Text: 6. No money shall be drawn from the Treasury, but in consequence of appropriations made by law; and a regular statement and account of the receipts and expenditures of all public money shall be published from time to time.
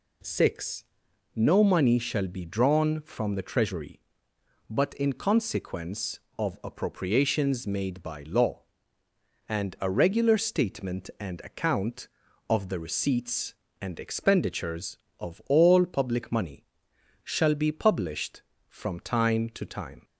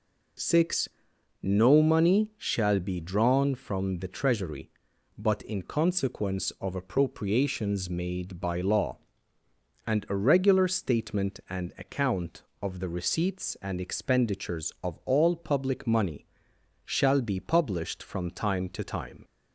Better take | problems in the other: neither | pauses between "money" and "shall"; noticeable; the same in both

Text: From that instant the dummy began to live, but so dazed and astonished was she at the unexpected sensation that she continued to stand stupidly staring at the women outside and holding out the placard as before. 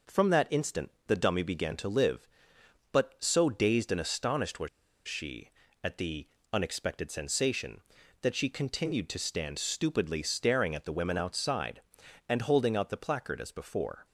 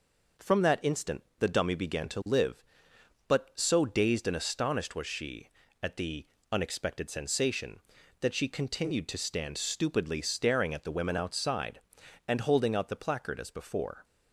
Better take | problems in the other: second | pauses between "instant" and "the"; slight; at 0.9 s; 0.16 s long; slight in the second // pauses between "was" and "she"; at 4.6 s; 0.39 s long // pauses between "the" and "unexpected"; slight; at 6.2 s; 0.24 s long; slight in the second

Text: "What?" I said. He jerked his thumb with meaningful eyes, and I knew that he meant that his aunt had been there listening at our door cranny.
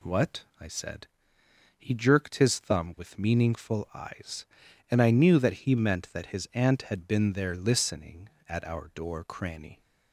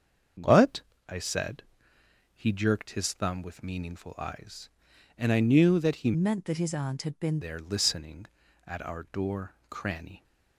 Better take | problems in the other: first | starts louder than the rest; until 2.3 s; 7 dB // changes voice from "meant" to "been"; from 6.1 to 7.3 s; 1.2 s long // pauses between "door" and "cranny"; slight; at 9.5 s; 0.16 s long

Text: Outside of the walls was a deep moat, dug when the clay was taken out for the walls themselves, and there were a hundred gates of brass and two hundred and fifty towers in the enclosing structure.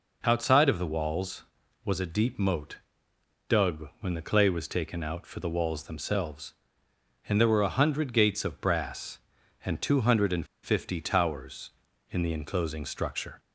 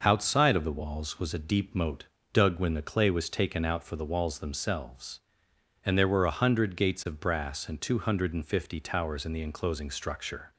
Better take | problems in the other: second | pauses between "and" and "fifty"; slight; at 10.4 s; 0.17 s long

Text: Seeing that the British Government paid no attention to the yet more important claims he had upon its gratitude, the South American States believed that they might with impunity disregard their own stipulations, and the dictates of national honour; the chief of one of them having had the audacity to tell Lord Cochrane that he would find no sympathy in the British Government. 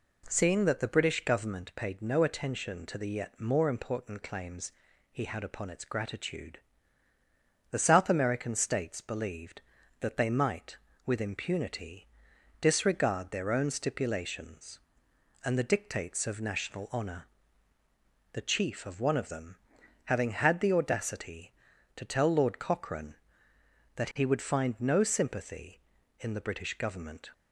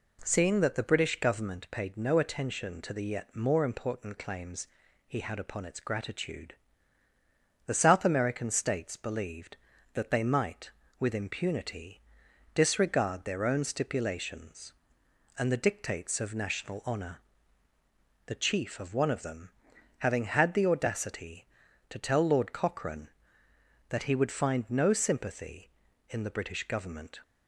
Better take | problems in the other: neither | pauses between "claims" and "he"; the same in both // pauses between "impunity" and "disregard"; noticeable; the same in both // pauses between "them" and "having"; noticeable; the same in both

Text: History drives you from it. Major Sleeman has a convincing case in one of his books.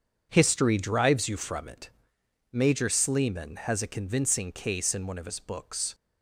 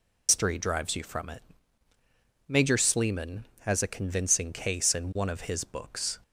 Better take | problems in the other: first | loses the start of "History"; at 0.2 s; 170 ms

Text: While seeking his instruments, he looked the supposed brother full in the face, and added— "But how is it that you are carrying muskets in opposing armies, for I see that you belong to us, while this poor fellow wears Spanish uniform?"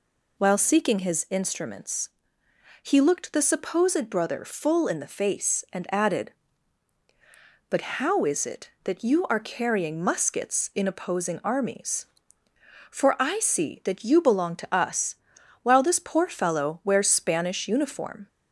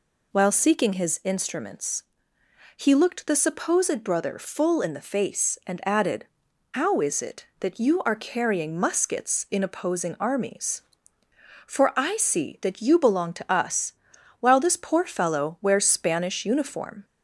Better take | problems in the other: first | skips "But"; at 6.4 s

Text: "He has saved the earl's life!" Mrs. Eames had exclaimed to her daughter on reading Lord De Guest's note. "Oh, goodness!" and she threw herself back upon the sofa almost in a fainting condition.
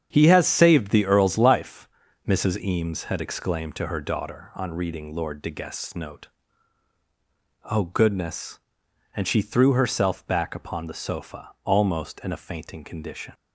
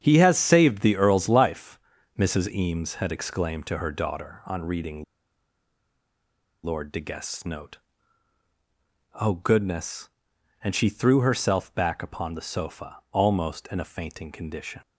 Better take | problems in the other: first | starts louder than the rest; strong; until 1.0 s; 8 dB; strong in the first // pauses between "reading" and "Lord"; strong; at 5.0 s; 1.6 s long

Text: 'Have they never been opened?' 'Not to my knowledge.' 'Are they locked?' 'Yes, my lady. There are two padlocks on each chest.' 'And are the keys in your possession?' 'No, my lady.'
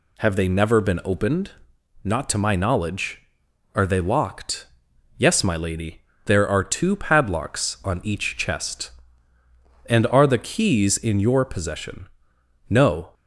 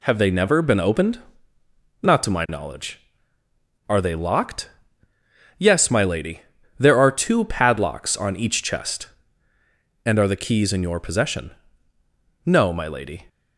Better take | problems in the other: second | stops before "my lady"; at 13.1 s

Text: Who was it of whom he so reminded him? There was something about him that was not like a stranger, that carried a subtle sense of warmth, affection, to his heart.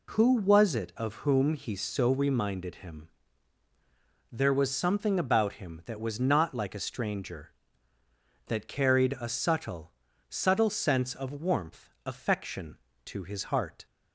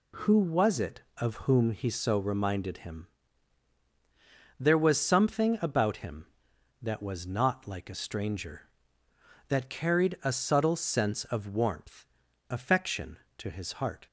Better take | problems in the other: second | says "subtle" twice; at 10.2 s

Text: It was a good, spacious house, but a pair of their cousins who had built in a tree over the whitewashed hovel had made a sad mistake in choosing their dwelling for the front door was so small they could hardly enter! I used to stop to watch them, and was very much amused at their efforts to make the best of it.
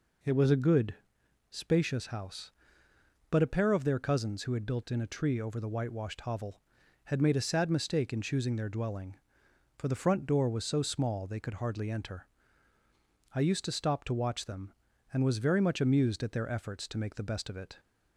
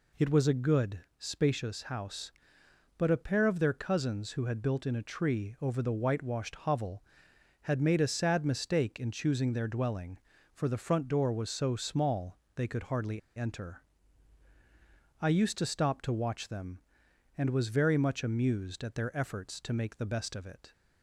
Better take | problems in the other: first | pauses between "small" and "they"; slight; at 12.3 s; 0.16 s long // pauses between "hardly" and "enter"; slight; at 13.1 s; 0.16 s long

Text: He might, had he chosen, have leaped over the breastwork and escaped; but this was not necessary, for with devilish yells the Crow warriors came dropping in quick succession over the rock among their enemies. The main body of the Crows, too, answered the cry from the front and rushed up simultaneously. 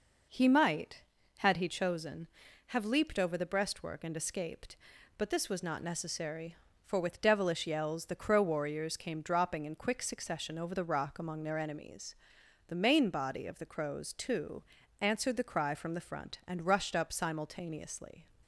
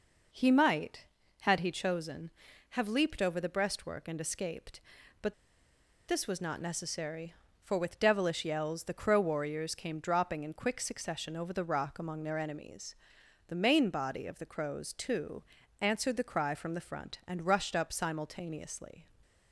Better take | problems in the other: first | pauses between "but" and "this"; noticeable; at 5.3 s; 0.74 s long

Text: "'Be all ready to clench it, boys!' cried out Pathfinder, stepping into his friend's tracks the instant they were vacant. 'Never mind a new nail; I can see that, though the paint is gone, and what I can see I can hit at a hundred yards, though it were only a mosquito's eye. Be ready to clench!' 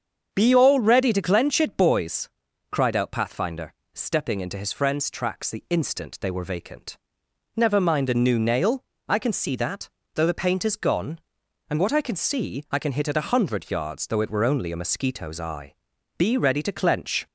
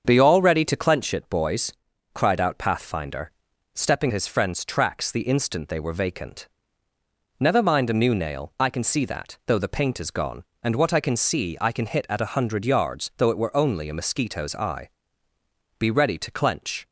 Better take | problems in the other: first | starts louder than the rest; until 1.0 s; 7 dB; strong in the first // skips "into"; at 4.1 s

